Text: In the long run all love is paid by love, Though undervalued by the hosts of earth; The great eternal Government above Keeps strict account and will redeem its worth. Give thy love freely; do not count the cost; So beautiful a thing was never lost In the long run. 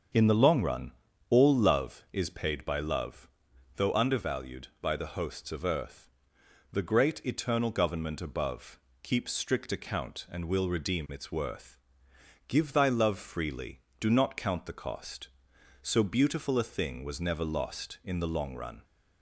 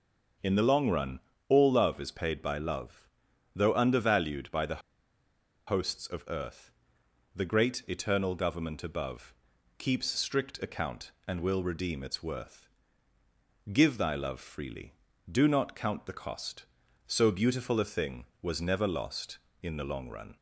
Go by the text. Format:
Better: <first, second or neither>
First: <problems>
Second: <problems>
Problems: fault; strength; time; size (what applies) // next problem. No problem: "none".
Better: first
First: starts louder than the rest; until 1.5 s; 7 dB // pauses between "run" and "all"; at 0.9 s; 0.40 s long // pauses between "above" and "Keeps"; slight; at 8.7 s; 0.22 s long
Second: starts louder than the rest; until 1.7 s; 6.5 dB // pauses between "run" and "all"; slight; at 1.1 s; 0.30 s long // pauses between "the" and "hosts"; noticeable; at 4.8 s; 0.89 s long // pauses between "above" and "Keeps"; noticeable; at 9.3 s; 0.46 s long